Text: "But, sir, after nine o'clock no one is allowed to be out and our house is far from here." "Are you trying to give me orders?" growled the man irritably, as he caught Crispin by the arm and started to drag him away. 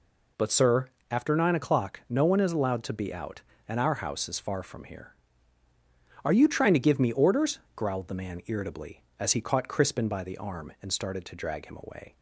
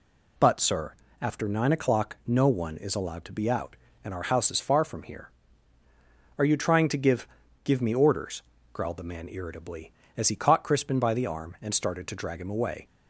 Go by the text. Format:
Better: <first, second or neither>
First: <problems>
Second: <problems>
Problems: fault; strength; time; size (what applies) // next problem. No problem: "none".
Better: first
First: none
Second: says "give" twice; at 7.6 s